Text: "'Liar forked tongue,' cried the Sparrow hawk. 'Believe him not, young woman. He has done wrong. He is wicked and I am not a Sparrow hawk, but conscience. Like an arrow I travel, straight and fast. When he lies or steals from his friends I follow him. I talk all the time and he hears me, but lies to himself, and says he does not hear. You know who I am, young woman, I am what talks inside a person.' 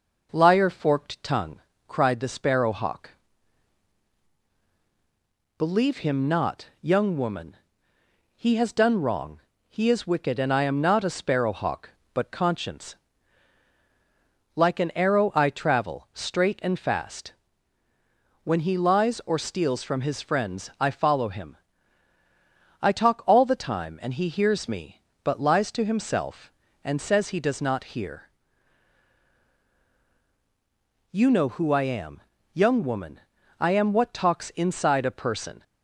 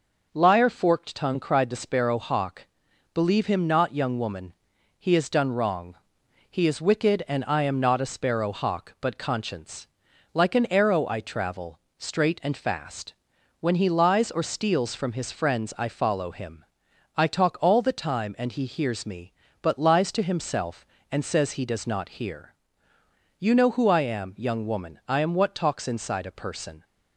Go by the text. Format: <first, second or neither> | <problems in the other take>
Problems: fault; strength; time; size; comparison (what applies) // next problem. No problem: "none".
neither | none